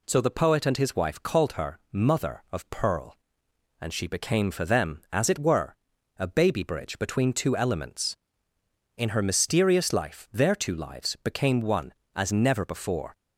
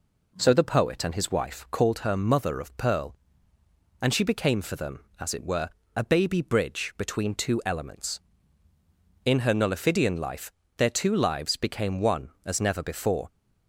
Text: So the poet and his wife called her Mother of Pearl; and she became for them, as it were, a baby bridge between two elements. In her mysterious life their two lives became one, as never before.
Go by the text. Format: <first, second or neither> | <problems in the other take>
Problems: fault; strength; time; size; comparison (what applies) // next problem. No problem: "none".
first | says "nullifidian" for "mysterious"; at 9.5 s // pauses between "life" and "their"; slight; at 10.5 s; 0.26 s long